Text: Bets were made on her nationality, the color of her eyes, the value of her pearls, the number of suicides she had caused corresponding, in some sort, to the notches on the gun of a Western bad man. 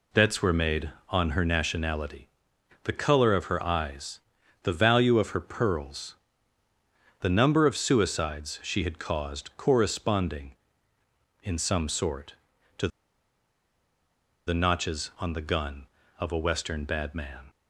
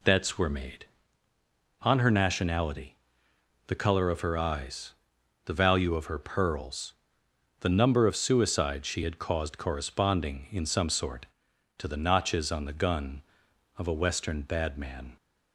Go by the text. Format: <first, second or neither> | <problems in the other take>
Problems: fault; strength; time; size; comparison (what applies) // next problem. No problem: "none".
second | pauses between "to" and "the"; strong; at 12.8 s; 1.5 s long